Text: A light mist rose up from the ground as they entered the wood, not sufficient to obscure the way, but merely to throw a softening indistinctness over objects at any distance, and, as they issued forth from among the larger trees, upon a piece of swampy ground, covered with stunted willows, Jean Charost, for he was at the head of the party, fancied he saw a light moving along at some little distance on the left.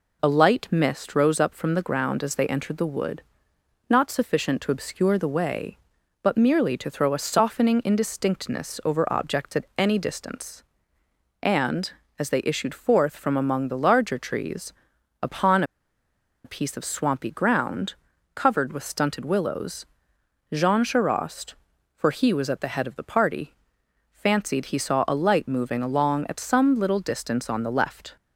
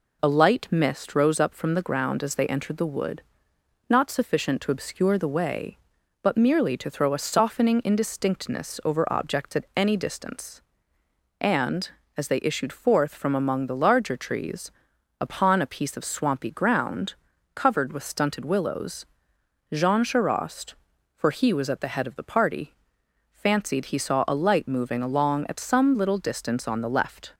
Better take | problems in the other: second | pauses between "upon" and "a"; noticeable; at 15.6 s; 0.81 s long

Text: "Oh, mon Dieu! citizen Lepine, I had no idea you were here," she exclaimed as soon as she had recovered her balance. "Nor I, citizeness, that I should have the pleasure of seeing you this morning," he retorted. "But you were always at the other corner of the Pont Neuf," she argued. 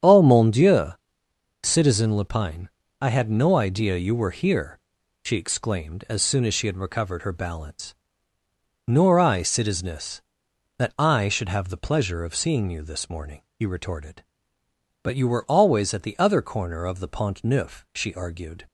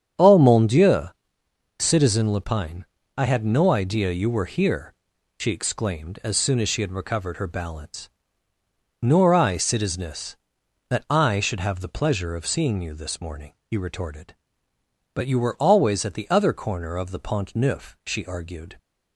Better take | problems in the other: neither | starts louder than the rest; strong; the same in both

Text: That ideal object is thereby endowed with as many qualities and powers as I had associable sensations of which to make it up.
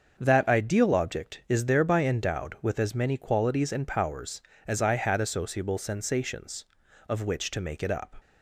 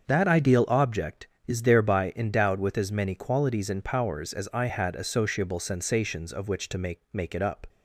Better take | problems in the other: first | starts louder than the rest; until 1.0 s; 6.5 dB; also in the first // says "make" twice; at 7.1 s

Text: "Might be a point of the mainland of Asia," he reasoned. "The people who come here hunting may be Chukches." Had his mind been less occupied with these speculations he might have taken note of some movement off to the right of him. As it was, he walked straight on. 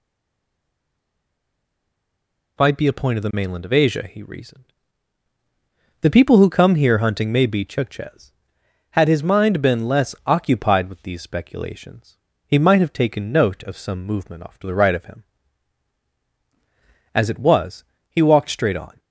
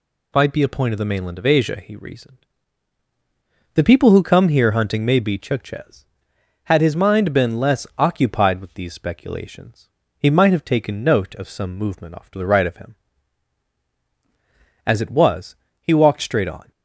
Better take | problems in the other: second | stays silent before the first word; strong; until 2.5 s; 2.5 s long // pauses between "speculations" and "he"; slight; at 12.1 s; 0.28 s long; slight in the second

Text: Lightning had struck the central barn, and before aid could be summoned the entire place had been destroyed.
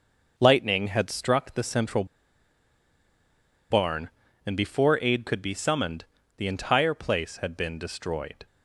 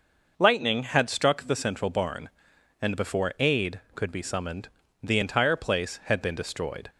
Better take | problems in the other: second | pauses between "central" and "barn"; strong; at 2.0 s; 1.6 s long // pauses between "summoned" and "the"; slight; at 6.0 s; 0.32 s long; slight in the second

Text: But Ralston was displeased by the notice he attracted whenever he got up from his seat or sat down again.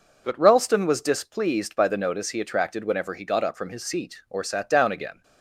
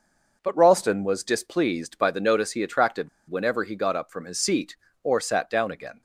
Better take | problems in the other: first | pauses between "attracted" and "whenever"; slight; at 3.0 s; 0.20 s long

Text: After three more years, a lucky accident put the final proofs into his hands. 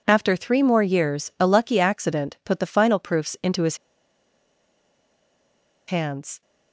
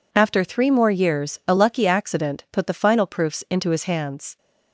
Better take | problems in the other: second | pauses between "his" and "hands"; strong; at 3.7 s; 2.1 s long

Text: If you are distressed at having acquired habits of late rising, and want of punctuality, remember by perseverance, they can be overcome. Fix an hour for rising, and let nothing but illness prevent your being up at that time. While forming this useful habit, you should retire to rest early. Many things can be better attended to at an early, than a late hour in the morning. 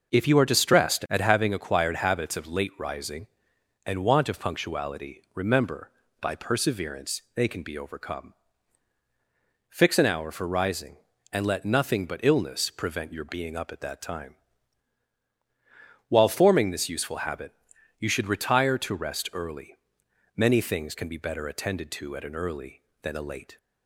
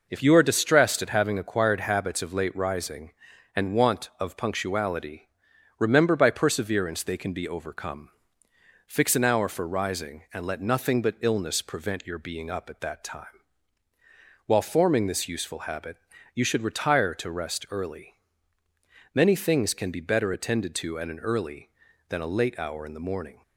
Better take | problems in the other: second | stops before "hour in the morning"; at 23.5 s

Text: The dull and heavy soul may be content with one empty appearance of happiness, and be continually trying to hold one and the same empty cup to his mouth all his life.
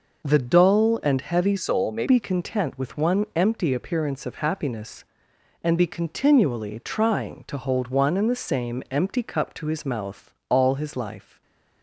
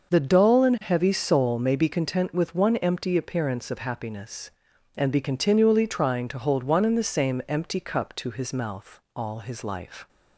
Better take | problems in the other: second | changes voice from "soul" to "may"; from 1.5 to 2.0 s; 0.5 s long // pauses between "mouth" and "all"; slight; at 10.3 s; 0.16 s long // stays silent after the last word; slight; from 11.2 s on; 0.6 s long

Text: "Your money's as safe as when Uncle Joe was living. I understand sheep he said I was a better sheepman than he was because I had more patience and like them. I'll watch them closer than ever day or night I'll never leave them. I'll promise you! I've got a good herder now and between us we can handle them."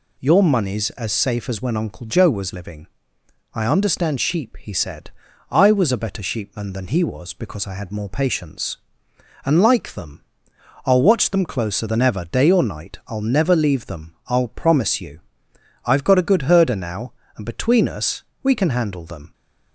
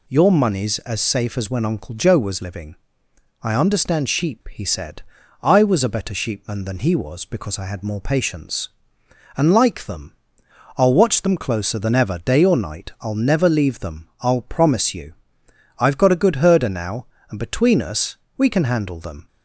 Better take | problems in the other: neither | pauses between "said" and "I"; the same in both // pauses between "us" and "we"; slight; the same in both

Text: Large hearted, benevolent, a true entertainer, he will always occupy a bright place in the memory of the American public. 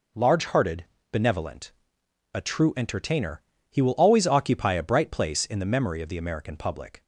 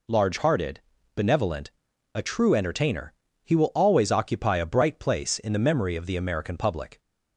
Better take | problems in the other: neither | none

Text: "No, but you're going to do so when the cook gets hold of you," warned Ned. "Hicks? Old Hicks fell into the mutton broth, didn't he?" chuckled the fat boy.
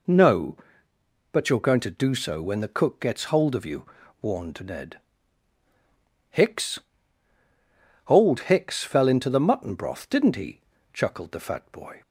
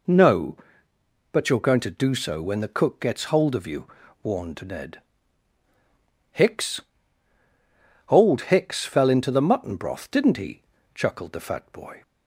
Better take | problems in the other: neither | none

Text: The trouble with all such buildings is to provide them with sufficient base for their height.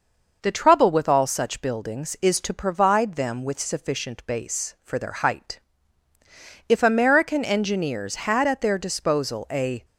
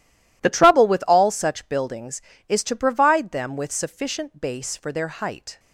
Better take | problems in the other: second | goes on to say "If American engineers had at their disposal a"; strong; from 6.6 s on; 3.1 s long

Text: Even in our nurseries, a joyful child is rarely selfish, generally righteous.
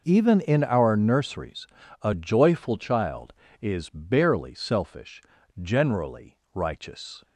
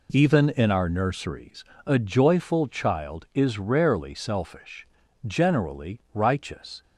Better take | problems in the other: second | says "barely" for "rarely"; at 3.8 s // pauses between "generally" and "righteous"; slight; at 6.3 s; 0.18 s long; slight in the second

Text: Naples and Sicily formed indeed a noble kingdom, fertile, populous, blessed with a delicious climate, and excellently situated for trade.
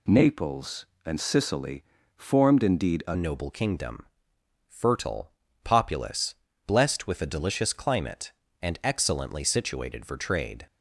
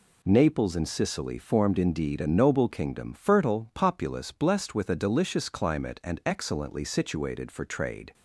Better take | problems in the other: second | pauses between "Sicily" and "formed"; slight; at 1.8 s; 0.32 s long // changes voice at "noble"; from 3.1 s on; 7.5 s long

